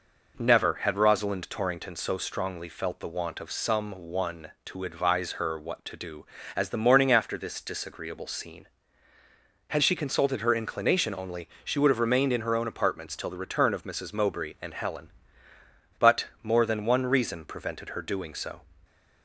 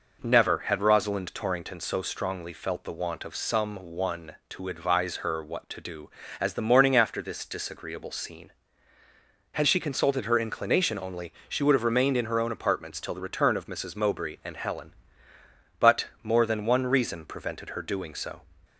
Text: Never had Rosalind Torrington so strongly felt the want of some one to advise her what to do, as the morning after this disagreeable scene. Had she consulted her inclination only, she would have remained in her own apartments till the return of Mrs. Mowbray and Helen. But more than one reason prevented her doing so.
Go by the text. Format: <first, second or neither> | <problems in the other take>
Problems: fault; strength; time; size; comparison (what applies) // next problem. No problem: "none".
neither | none